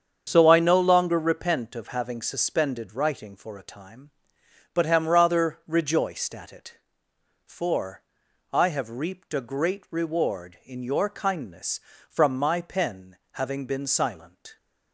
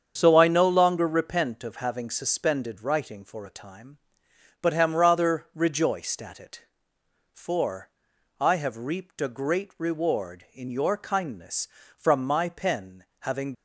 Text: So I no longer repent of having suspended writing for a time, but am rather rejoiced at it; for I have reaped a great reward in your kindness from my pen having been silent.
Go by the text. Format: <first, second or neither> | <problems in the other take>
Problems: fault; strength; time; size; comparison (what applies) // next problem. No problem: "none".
first | starts louder than the rest; strong; until 1.2 s; 7.5 dB; strong in the first // pauses between "for" and "I"; noticeable; at 7.8 s; 0.50 s long; noticeable in the first // pauses between "pen" and "having"; slight; at 13.0 s; 0.20 s long; slight in the first // stops before "been silent"; at 13.5 s